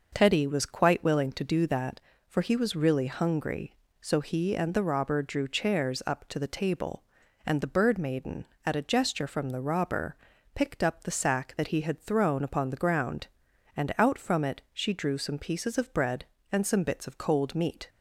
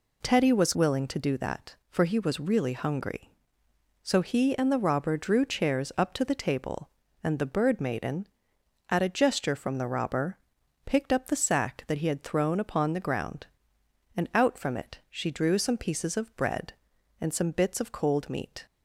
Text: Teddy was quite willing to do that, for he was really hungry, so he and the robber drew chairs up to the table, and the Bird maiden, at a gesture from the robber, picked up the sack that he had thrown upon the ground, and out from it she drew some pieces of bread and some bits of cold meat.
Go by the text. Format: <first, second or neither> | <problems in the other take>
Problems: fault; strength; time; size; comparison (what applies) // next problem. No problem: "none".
first | skips "quite"; at 0.7 s